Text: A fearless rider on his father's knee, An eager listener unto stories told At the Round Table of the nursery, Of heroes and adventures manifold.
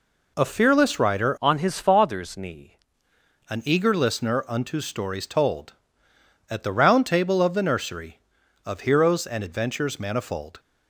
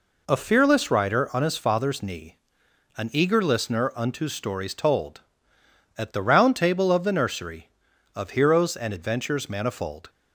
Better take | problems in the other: second | changes voice from "on" to "knee"; from 1.4 to 2.7 s; 1.3 s long

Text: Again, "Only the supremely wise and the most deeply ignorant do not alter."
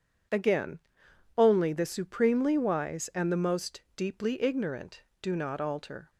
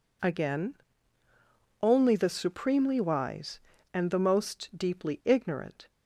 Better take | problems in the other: first | stops before "do not alter"; at 5.8 s

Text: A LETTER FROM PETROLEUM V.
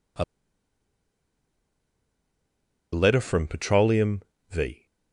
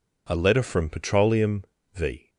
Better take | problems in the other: second | pauses between "A" and "LETTER"; strong; at 0.2 s; 2.6 s long // pauses between "PETROLEUM" and "V"; slight; at 4.2 s; 0.30 s long; slight in the second

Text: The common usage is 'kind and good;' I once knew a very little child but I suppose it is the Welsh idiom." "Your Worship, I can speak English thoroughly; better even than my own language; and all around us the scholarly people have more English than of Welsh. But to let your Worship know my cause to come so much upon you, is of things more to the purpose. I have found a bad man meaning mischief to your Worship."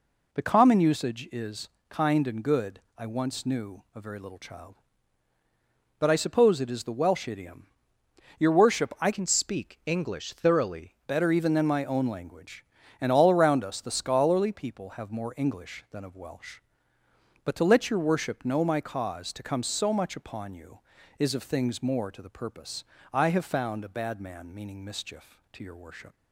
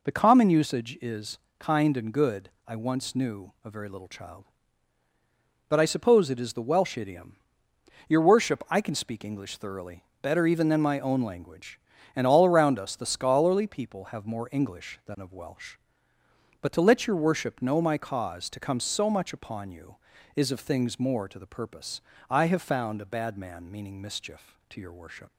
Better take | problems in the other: second | pauses between "is" and "kind"; slight; at 1.6 s; 0.22 s long; slight in the second // changes voice from "can" to "thoroughly"; from 9.1 to 10.9 s; 1.8 s long

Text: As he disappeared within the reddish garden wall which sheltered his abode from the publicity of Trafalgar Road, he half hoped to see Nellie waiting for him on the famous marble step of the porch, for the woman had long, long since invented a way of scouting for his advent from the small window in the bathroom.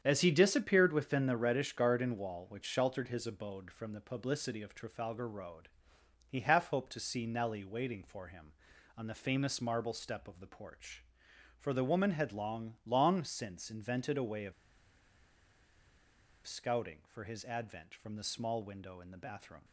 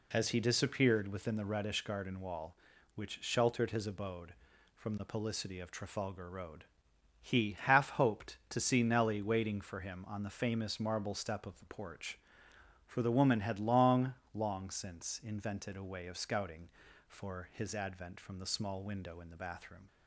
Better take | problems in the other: second | starts louder than the rest; strong; until 1.0 s; 8.5 dB // pauses between "of" and "scouting"; strong; at 14.5 s; 1.9 s long

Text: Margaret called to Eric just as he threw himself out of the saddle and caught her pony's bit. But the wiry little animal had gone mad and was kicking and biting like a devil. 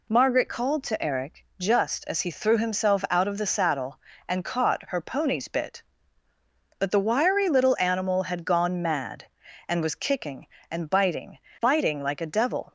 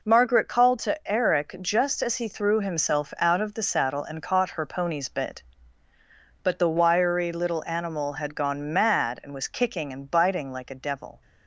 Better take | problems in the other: second | says "biting" twice; at 11.6 s

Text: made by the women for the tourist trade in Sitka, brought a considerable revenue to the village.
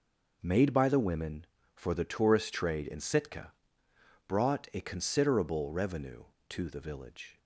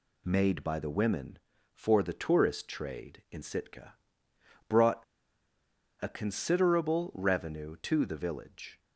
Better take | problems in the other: first | pauses between "brought" and "a"; at 5.0 s; 0.98 s long

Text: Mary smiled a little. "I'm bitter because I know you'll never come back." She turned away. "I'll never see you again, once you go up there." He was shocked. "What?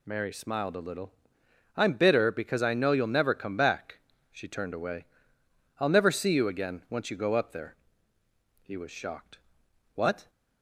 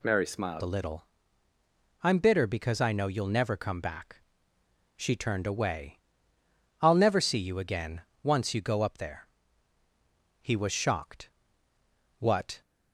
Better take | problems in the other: first | changes voice at "a"; from 0.6 s on; 12.0 s long

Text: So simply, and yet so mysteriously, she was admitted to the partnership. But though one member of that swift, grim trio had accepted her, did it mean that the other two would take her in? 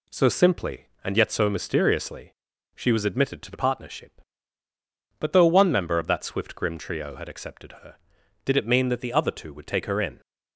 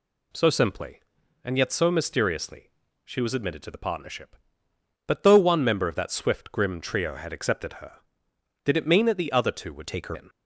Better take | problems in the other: first | changes voice from "take" to "her"; from 9.8 to 10.1 s; 0.3 s long

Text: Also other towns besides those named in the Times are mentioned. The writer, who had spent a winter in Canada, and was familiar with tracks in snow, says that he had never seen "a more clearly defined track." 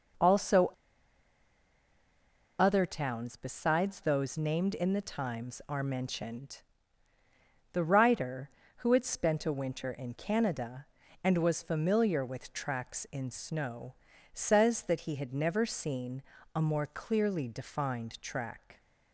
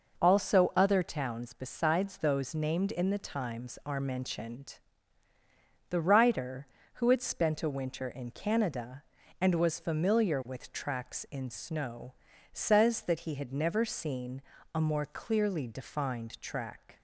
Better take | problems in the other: second | pauses between "Also" and "other"; strong; at 0.7 s; 1.8 s long // pauses between "seen" and "a"; slight; at 16.2 s; 0.34 s long; slight in the second

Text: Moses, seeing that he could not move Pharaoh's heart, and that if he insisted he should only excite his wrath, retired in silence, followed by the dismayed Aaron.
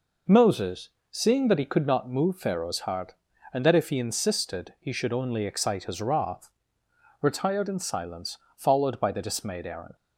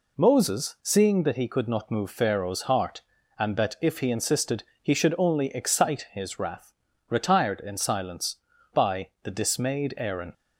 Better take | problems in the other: first | pauses between "insisted" and "he"; slight; at 4.6 s; 0.20 s long // skips "followed"; at 8.5 s

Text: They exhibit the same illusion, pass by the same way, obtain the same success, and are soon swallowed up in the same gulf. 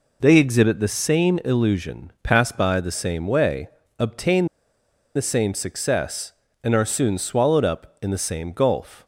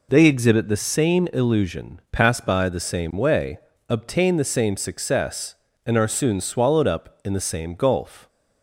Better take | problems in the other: second | pauses between "obtain" and "the"; noticeable; at 4.4 s; 0.70 s long

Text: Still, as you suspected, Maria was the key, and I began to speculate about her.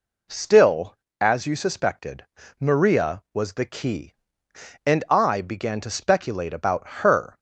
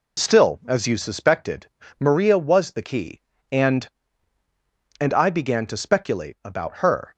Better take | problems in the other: first | says "and" twice; at 5.0 s

